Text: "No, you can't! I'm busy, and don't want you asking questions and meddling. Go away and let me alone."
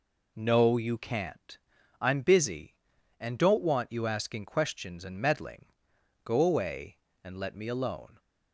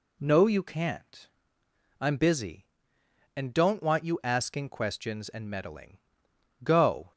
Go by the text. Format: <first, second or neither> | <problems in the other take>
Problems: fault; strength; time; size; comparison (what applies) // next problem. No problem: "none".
first | stops before "away and let me alone"; at 7.1 s